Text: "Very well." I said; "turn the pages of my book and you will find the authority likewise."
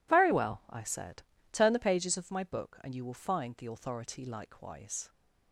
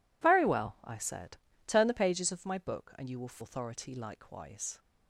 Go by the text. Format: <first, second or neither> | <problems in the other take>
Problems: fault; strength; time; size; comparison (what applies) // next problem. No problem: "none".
first | skips "find the"; at 3.4 s